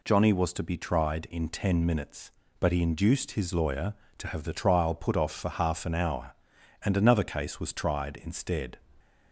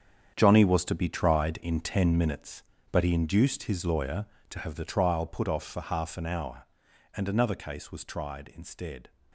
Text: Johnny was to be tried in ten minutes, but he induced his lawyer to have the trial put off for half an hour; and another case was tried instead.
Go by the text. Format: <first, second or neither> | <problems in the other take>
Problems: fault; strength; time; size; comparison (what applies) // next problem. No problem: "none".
first | gets quieter; strong; throughout; 12 dB